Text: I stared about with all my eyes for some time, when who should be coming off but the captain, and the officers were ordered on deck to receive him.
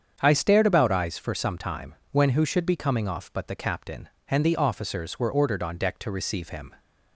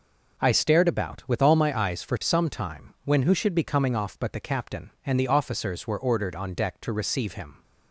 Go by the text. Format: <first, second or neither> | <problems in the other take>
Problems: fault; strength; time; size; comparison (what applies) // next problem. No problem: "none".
second | starts louder than the rest; strong; until 1.2 s; 7.5 dB // skips "with all my"; at 0.9 s